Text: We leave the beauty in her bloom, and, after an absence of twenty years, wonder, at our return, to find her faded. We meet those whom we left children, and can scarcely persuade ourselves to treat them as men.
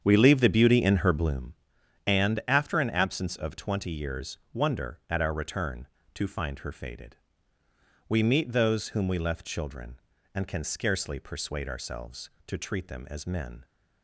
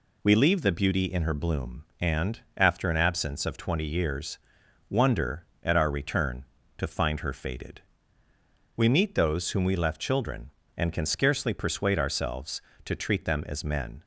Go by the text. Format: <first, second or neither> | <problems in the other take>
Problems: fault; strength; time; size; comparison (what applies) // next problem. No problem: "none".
second | starts louder than the rest; strong; until 1.5 s; 8 dB